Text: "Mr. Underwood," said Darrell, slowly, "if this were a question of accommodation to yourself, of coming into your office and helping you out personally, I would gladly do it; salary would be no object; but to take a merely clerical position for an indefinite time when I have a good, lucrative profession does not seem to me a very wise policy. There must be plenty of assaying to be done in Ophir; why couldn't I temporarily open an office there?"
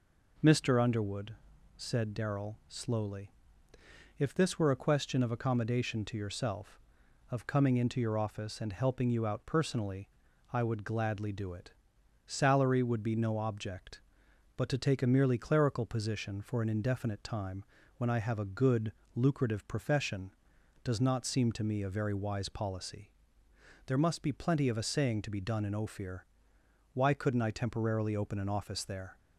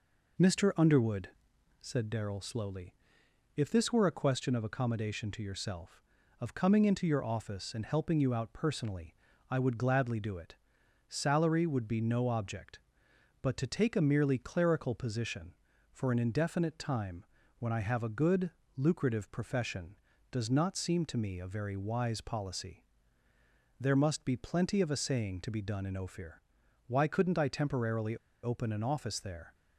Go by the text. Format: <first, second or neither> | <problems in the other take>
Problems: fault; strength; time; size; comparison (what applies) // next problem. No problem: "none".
first | pauses between "time" and "when"; slight; at 17.2 s; 0.32 s long; slight in the first // pauses between "temporarily" and "open"; slight; at 28.1 s; 0.26 s long